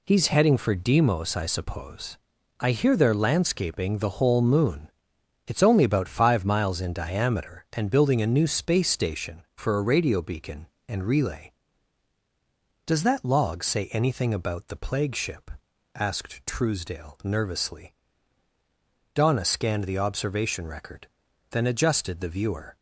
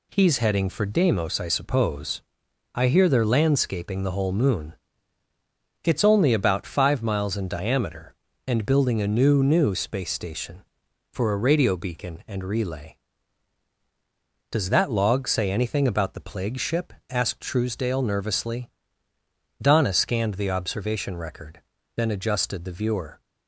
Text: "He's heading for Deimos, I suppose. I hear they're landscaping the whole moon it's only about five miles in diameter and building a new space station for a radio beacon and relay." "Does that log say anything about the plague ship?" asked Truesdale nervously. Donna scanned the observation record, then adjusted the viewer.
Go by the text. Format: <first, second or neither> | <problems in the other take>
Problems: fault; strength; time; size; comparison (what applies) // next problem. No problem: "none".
first | pauses between "moon" and "it's"; at 4.7 s; 1.0 s long; noticeable in the first // says "new" twice; at 9.4 s